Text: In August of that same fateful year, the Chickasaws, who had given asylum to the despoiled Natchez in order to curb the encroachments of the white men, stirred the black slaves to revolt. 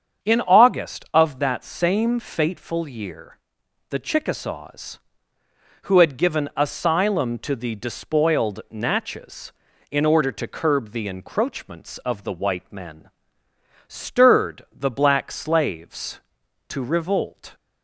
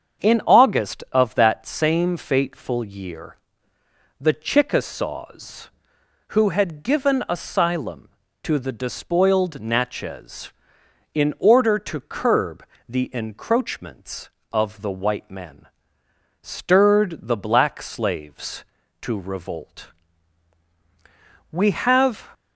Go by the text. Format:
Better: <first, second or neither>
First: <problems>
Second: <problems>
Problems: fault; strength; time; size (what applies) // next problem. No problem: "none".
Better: first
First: starts louder than the rest; strong; until 1.3 s; 7 dB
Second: starts louder than the rest; strong; until 1.3 s; 7 dB // pauses between "curb" and "the"; slight; at 12.6 s; 0.24 s long // goes on to say "We have"; noticeable; from 21.5 s on; 0.80 s long